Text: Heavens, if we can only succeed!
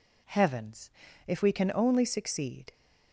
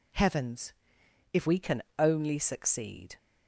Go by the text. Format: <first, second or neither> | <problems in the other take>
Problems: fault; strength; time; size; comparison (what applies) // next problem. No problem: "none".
first | changes voice at "we"; from 1.4 s on; 1.7 s long // pauses between "can" and "only"; slight; at 1.8 s; 0.16 s long